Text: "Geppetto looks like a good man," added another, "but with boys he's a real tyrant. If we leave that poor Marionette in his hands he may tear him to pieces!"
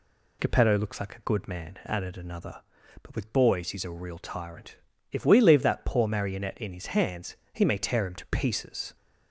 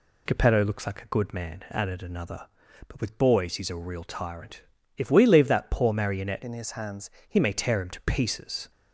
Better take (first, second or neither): first